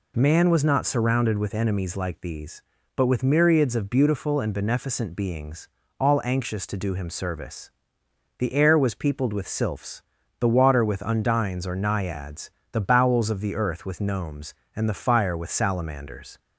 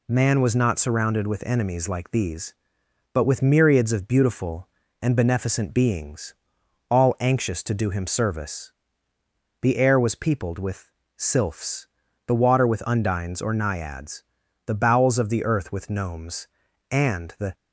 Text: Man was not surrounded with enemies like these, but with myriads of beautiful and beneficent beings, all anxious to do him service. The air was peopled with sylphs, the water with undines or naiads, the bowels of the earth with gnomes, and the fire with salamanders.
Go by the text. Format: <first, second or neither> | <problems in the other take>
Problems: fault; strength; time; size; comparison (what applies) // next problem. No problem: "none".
first | pauses between "with" and "sylphs"; slight; at 10.8 s; 0.26 s long // stops before "fire with salamanders"; at 17.5 s